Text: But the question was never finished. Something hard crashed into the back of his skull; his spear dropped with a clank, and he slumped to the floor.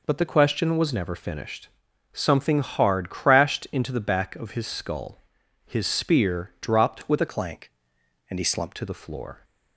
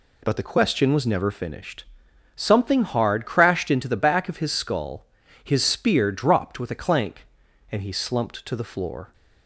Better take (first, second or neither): second